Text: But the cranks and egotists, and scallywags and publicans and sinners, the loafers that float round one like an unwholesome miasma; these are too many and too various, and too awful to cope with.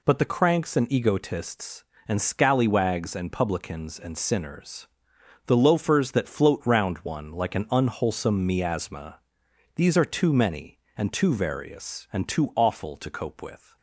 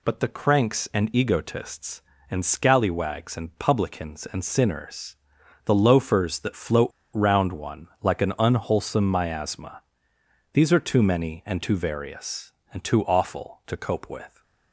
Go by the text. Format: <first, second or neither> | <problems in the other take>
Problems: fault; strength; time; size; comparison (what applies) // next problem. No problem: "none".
first | pauses between "float" and "round"; slight; at 6.9 s; 0.24 s long // pauses between "one" and "like"; slight; at 7.8 s; 0.16 s long